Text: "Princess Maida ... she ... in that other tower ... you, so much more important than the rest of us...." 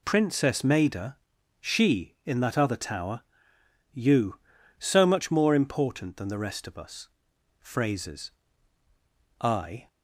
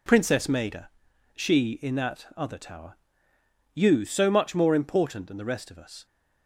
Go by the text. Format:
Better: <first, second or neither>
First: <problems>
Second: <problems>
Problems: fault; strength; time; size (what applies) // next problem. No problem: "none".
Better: second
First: goes on to say "Phrases I"; strong; from 7.6 s on; 2.2 s long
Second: none